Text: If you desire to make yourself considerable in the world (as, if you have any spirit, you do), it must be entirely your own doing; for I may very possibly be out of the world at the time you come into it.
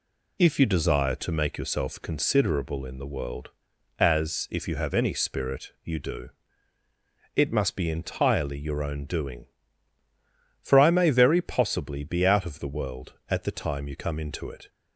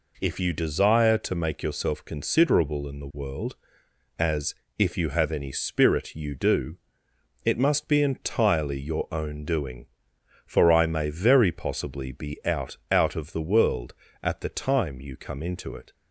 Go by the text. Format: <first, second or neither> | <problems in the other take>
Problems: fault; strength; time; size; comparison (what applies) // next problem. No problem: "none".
first | says "out" twice; at 12.9 s